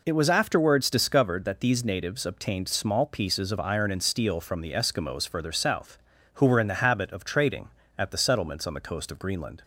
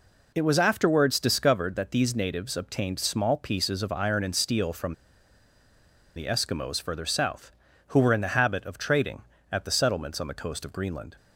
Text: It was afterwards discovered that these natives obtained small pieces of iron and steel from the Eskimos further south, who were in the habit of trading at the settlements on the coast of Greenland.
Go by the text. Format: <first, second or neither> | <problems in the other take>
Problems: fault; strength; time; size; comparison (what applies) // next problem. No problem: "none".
first | pauses between "from" and "the"; at 4.9 s; 1.2 s long